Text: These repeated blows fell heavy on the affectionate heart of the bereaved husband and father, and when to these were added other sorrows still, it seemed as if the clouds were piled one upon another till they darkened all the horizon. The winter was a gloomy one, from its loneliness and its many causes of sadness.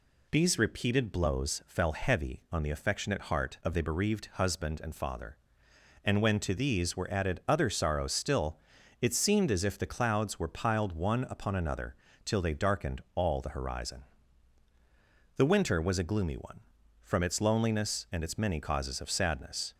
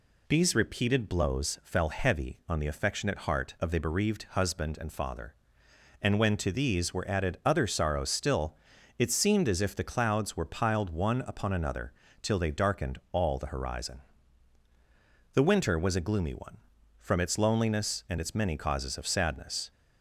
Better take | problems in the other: neither | pauses between "another" and "till"; slight; the same in both

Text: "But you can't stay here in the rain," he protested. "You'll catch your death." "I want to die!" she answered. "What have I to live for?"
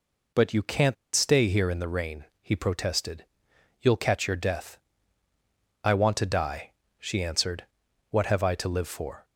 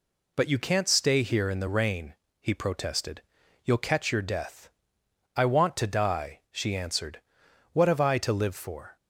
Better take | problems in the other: second | pauses between "can't" and "stay"; slight; at 0.9 s; 0.19 s long

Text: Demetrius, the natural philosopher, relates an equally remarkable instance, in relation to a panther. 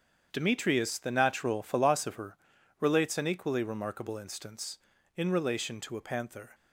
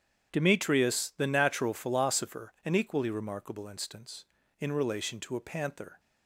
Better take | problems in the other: first | starts louder than the rest; strong; until 1.3 s; 9 dB; strong in the first // skips "relates"; at 2.5 s

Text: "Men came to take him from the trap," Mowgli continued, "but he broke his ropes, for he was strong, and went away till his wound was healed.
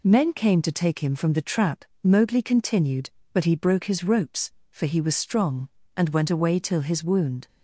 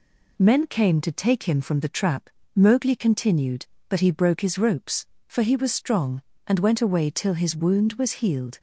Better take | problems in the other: second | stops before "was healed"; at 7.4 s

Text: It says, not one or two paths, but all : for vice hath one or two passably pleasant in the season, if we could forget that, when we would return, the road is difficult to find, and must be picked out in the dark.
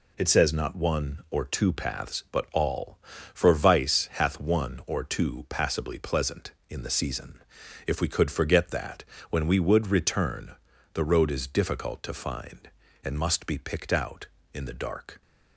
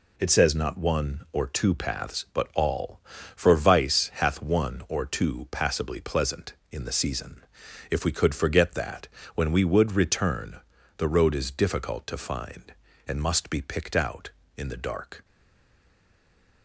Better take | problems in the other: first | stays silent after the last word; noticeable; from 15.2 s on; 1.4 s long

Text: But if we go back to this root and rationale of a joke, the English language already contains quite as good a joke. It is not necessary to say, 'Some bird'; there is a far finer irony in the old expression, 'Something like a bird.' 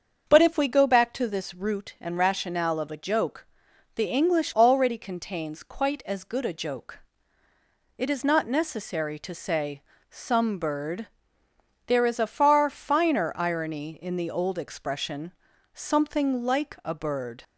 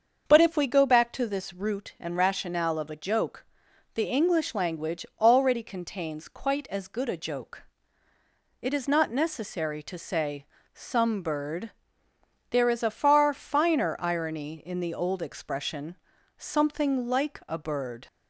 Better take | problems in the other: second | starts louder than the rest; until 1.2 s; 7 dB; also in the second // skips "language"; at 4.5 s

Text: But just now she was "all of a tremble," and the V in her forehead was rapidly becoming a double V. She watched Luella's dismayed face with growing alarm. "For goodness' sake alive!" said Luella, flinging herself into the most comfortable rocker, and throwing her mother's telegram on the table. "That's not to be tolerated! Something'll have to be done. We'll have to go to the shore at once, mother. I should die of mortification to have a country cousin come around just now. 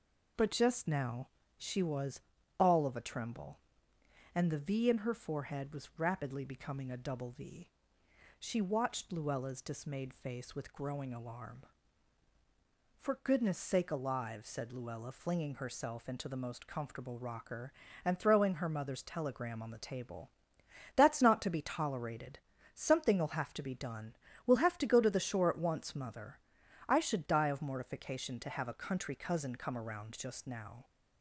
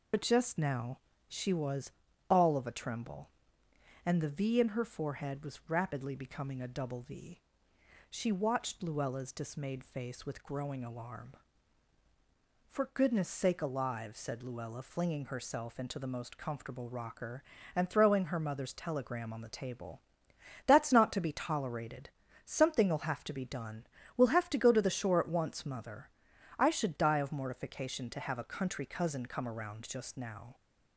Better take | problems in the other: first | loses the start of "But"; at 0.1 s; 60 ms // pauses between "now" and "she"; slight; at 0.9 s; 0.28 s long; slight in the first // pauses between "was" and "all"; at 1.9 s; 0.38 s long; also in the first

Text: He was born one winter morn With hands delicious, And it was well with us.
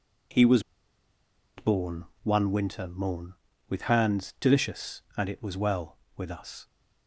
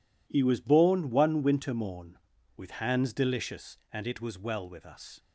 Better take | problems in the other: second | pauses between "was" and "born"; noticeable; at 0.6 s; 0.95 s long // pauses between "born" and "one"; slight; at 2.0 s; 0.18 s long

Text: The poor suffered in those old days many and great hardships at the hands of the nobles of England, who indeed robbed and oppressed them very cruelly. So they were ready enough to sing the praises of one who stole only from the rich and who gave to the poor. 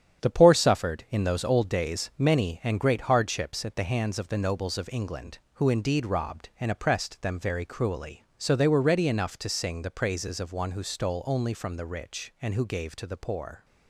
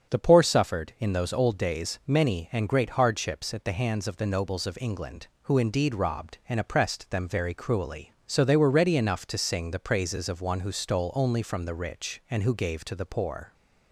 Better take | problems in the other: second | gets quieter; throughout; 7 dB // starts louder than the rest; strong; until 1.2 s; 9 dB; strong in the second

